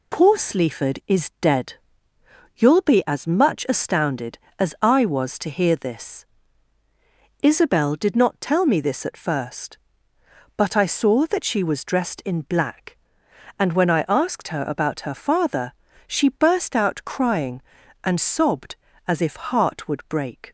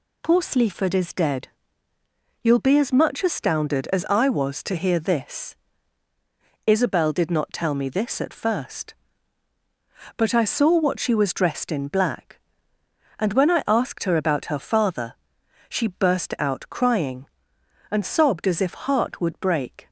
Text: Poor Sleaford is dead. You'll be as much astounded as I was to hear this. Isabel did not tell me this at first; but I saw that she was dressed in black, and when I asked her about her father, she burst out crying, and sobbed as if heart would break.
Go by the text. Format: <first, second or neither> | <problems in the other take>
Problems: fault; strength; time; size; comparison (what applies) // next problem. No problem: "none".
first | says "what" for "that"; at 10.7 s